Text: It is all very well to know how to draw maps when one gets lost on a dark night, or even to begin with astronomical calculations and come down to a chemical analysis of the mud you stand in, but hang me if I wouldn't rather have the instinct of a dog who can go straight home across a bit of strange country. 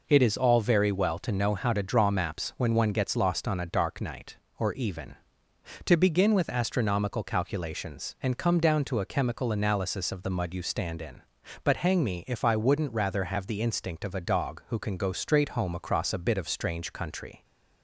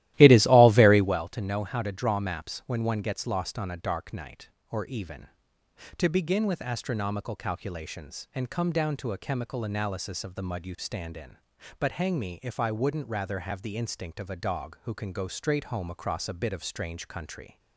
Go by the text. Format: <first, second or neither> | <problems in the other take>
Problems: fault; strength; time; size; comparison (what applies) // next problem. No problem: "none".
first | starts louder than the rest; strong; until 1.2 s; 15 dB